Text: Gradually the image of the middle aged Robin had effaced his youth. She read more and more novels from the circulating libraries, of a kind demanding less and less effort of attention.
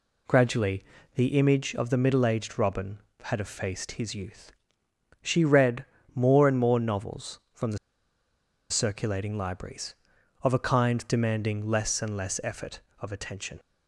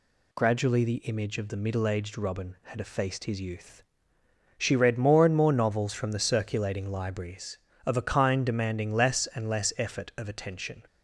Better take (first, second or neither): second